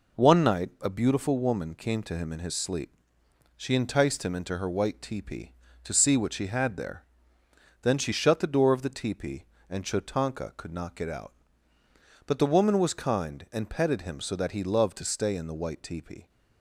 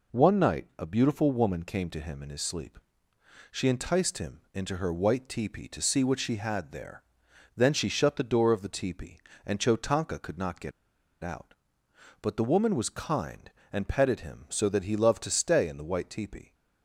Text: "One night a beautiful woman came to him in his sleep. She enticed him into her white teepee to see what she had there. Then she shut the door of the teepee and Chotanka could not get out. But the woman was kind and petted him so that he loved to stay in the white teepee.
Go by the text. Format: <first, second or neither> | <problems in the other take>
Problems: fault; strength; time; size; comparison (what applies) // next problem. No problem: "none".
first | pauses between "get" and "out"; noticeable; at 10.7 s; 0.52 s long